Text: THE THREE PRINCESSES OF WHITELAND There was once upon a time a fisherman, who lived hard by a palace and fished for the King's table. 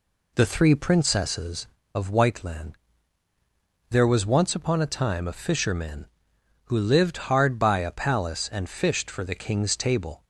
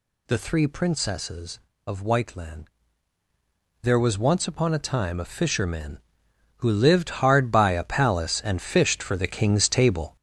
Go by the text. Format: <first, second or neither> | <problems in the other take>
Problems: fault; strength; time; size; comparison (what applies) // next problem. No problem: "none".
first | gets louder; throughout; 6.5 dB // pauses between "WHITELAND" and "There"; at 2.6 s; 1.1 s long; also in the first